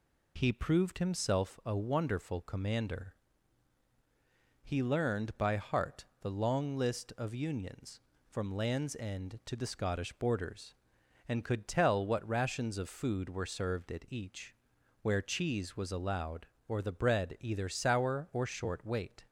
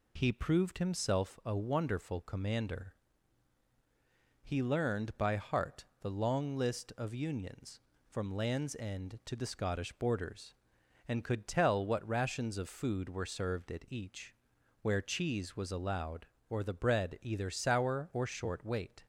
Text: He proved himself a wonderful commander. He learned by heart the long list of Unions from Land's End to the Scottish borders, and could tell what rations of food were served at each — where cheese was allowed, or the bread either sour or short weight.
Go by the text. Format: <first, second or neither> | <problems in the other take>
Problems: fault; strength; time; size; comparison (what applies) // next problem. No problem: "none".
neither | pauses between "heart" and "the"; slight; the same in both